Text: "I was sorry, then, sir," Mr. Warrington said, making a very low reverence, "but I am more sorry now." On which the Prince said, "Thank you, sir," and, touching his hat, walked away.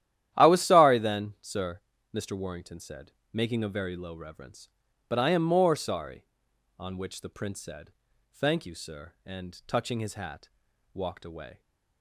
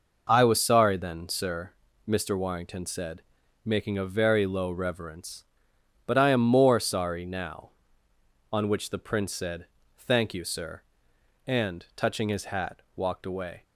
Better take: second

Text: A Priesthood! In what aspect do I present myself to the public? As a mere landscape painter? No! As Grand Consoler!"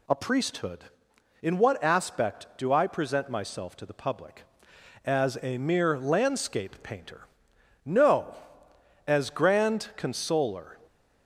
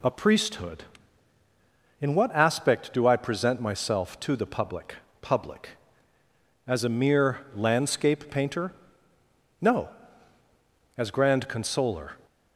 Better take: first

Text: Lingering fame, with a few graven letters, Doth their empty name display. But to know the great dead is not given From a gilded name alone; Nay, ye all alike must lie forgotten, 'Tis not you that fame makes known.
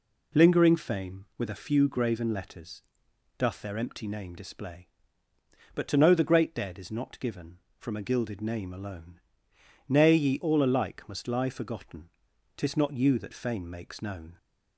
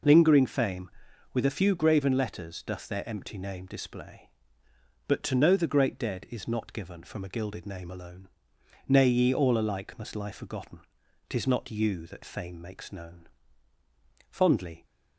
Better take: first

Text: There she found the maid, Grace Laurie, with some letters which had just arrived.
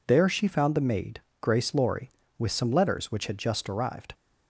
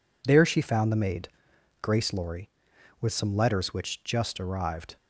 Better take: first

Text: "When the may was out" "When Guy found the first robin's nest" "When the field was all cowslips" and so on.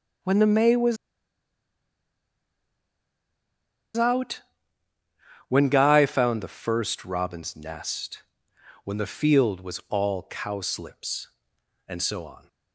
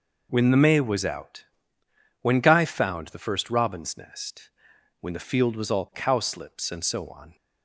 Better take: second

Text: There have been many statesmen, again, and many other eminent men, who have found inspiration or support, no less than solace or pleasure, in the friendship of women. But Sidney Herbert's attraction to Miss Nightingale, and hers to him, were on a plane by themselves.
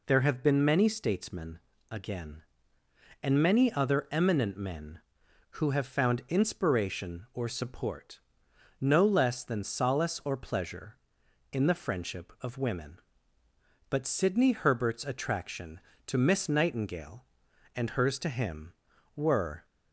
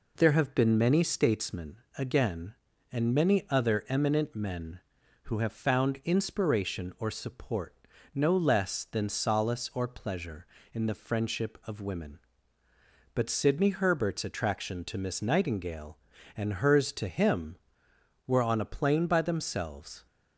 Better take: second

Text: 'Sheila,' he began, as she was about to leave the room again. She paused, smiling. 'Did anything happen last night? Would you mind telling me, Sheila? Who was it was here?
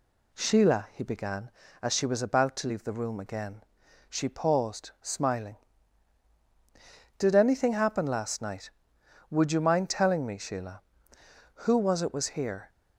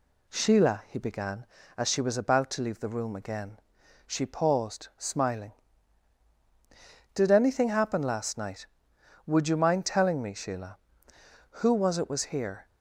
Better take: neither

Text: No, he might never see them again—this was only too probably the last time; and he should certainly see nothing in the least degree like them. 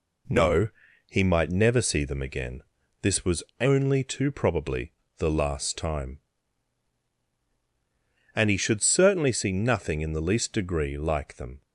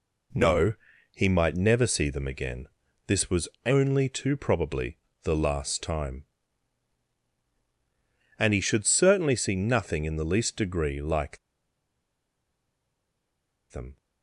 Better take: first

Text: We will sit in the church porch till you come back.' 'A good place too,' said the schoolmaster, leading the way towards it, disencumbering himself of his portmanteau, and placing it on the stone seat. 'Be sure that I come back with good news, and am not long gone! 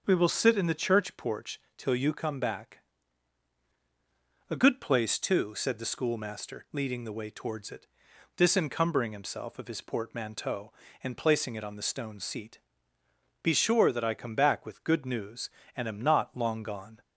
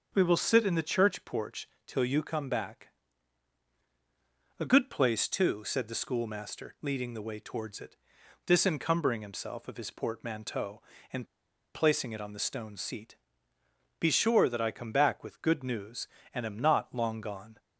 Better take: first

